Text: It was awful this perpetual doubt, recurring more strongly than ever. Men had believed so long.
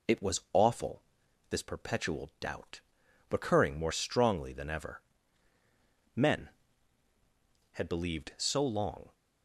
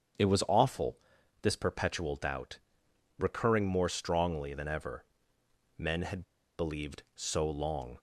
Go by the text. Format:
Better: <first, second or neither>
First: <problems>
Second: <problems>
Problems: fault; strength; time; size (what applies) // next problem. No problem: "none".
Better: first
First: pauses between "awful" and "this"; noticeable; at 1.0 s; 0.48 s long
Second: starts louder than the rest; strong; until 1.6 s; 8 dB // pauses between "awful" and "this"; at 0.9 s; 0.44 s long // pauses between "had" and "believed"; slight; at 6.2 s; 0.35 s long